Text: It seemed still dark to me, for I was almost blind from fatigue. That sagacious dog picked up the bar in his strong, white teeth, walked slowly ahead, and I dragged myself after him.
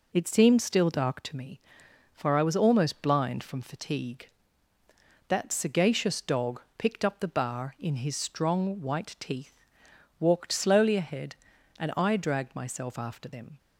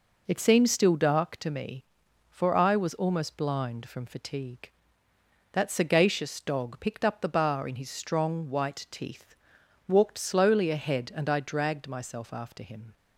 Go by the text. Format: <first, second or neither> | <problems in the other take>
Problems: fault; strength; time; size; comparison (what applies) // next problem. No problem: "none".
second | pauses between "dog" and "picked"; slight; at 6.6 s; 0.16 s long // says "them" for "him"; at 13.2 s